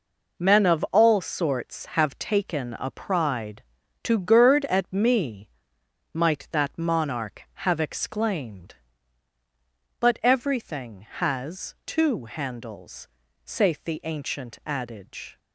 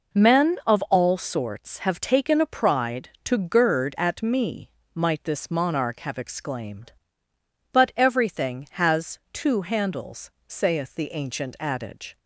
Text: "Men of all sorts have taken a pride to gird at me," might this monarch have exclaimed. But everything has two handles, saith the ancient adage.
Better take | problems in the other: second | says "that" for "this"; at 6.5 s

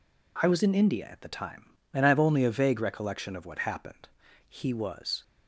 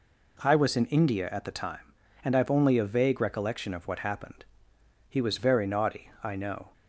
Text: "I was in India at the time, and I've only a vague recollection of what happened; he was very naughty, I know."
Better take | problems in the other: second | stops before "very naughty I know"; at 5.2 s

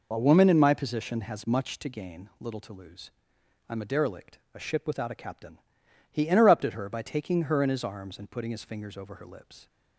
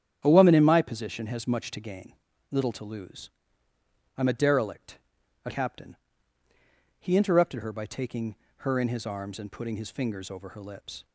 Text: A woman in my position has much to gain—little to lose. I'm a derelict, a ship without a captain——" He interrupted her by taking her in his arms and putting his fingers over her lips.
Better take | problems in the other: first | starts louder than the rest; strong; until 1.2 s; 9.5 dB // skips "ship without a"; at 5.5 s // pauses between "taking" and "her"; slight; at 8.3 s; 0.22 s long

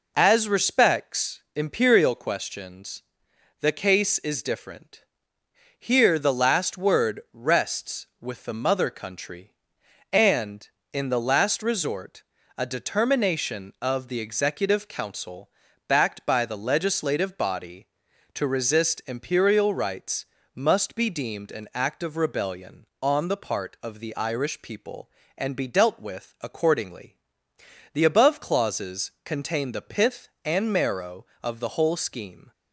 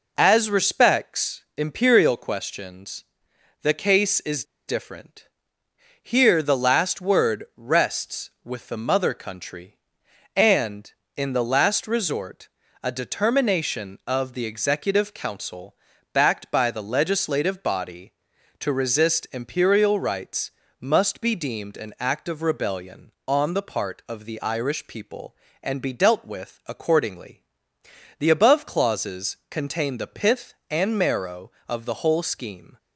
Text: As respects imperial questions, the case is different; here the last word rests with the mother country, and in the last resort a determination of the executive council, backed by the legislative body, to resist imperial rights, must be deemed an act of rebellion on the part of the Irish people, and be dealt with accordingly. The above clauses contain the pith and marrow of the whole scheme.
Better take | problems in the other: first | pauses between "respects" and "imperial"; slight; at 1.4 s; 0.16 s long; slight in the first // pauses between "is" and "different"; slight; at 4.4 s; 0.24 s long // pauses between "resort" and "a"; slight; at 12.4 s; 0.34 s long; slight in the first

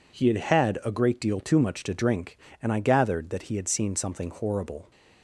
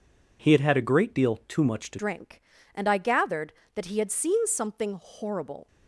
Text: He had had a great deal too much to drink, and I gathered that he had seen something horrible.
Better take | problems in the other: first | changes voice at "drink"; from 1.9 s on; 3.7 s long

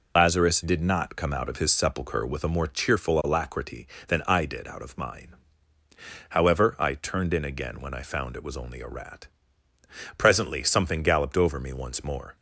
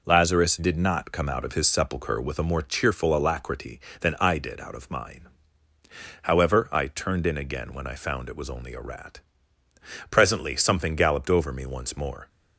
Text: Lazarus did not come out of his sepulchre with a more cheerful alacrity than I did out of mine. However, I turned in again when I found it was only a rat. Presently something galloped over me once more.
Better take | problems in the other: second | loses the start of "Lazarus"; at 0.1 s; 60 ms

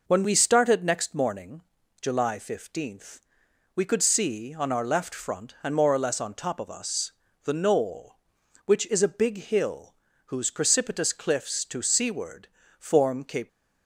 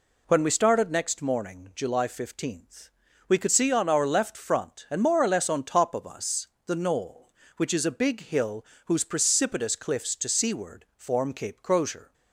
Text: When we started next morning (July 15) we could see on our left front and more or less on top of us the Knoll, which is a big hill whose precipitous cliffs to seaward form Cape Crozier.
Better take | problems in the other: second | pauses between "us" and "the"; slight; at 7.1 s; 0.32 s long; slight in the second // pauses between "hill" and "whose"; slight; at 9.9 s; 0.30 s long; slight in the second // pauses between "seaward" and "form"; slight; at 12.4 s; 0.32 s long // stops before "Crozier"; at 13.4 s

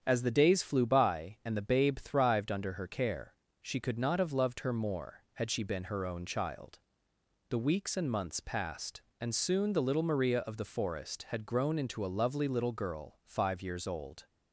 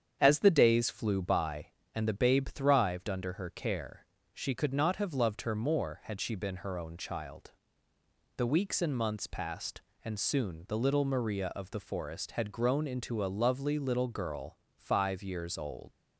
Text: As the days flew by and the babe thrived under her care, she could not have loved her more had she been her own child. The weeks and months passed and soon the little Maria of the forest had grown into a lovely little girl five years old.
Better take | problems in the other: first | starts louder than the rest; strong; until 1.2 s; 8 dB; strong in the first // pauses between "girl" and "five"; slight; at 14.5 s; 0.18 s long // leaves "old" unfinished; at 15.9 s; 105 ms

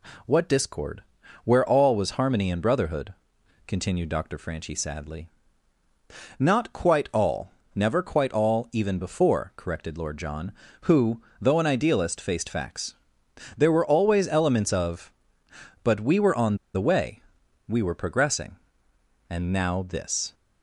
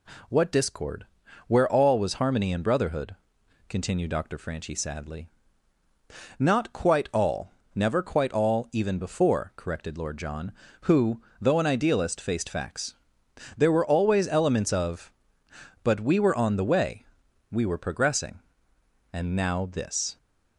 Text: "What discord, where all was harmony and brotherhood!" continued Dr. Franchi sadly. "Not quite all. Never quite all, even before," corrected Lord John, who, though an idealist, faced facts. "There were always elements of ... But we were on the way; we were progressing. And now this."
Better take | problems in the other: second | pauses between "on" and "the"; slight; at 16.5 s; 0.19 s long

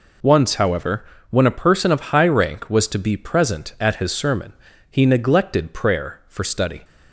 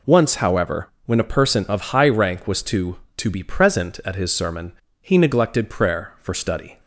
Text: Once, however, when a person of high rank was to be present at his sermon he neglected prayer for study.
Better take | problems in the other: first | says "to" twice; at 3.1 s // pauses between "sermon" and "he"; slight; at 4.7 s; 0.30 s long; slight in the first

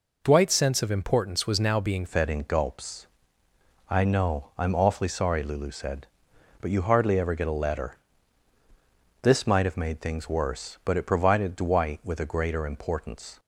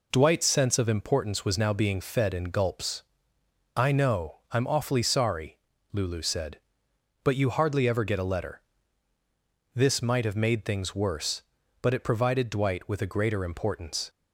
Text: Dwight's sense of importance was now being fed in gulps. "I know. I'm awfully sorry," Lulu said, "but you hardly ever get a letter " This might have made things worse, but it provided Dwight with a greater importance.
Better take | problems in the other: second | changes voice at "fed"; from 2.0 s on; 11.3 s long

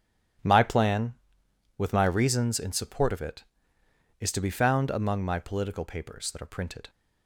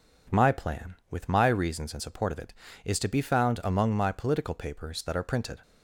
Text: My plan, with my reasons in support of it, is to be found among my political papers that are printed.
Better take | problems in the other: second | gets quieter; strong; throughout; 11.5 dB

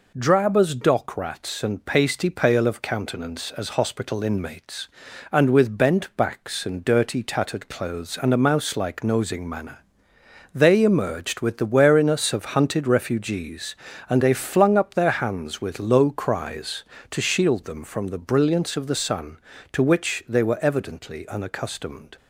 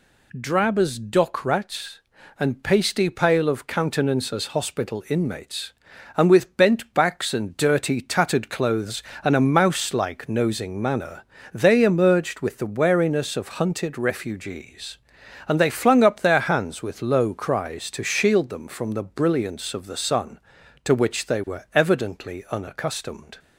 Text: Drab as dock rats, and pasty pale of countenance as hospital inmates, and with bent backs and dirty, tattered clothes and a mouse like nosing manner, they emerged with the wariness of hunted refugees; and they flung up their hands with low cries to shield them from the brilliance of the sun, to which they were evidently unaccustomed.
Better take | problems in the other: neither | none

